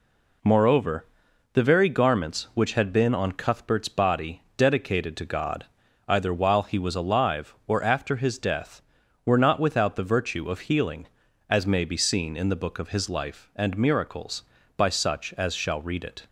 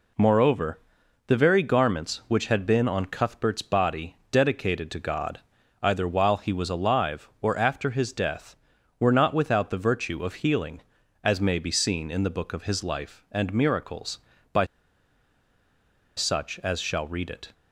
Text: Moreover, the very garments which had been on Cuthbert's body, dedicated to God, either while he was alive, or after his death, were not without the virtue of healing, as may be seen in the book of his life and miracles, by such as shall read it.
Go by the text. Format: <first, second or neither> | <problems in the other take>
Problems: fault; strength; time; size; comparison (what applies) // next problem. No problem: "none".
first | pauses between "by" and "such"; strong; at 14.6 s; 1.5 s long